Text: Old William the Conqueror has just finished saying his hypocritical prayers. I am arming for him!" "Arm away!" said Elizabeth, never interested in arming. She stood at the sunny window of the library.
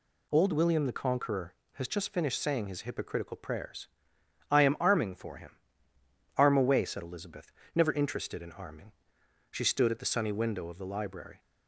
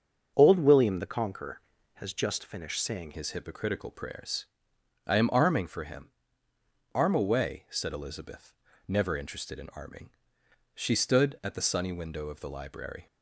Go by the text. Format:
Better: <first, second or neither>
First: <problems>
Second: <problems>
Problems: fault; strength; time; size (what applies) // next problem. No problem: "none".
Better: first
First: none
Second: starts louder than the rest; until 1.3 s; 6.5 dB // changes voice at "his"; from 3.1 s on; 9.9 s long